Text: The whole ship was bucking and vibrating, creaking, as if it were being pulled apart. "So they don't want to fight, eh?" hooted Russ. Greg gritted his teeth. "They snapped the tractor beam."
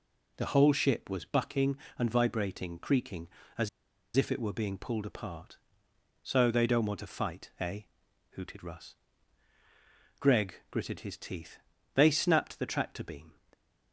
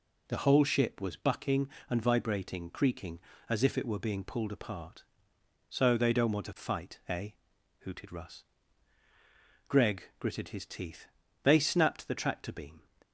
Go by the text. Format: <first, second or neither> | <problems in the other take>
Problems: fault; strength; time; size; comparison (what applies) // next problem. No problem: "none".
second | pauses between "as" and "if"; noticeable; at 3.6 s; 0.48 s long // pauses between "Greg" and "gritted"; slight; at 10.5 s; 0.16 s long; slight in the second